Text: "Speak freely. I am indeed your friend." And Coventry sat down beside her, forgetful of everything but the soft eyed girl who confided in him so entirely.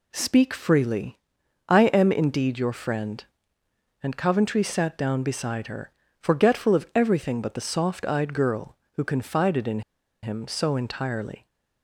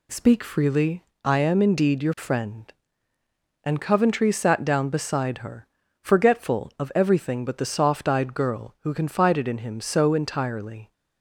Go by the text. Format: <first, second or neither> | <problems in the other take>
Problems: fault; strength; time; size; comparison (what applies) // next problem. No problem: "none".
second | pauses between "in" and "him"; at 9.8 s; 0.42 s long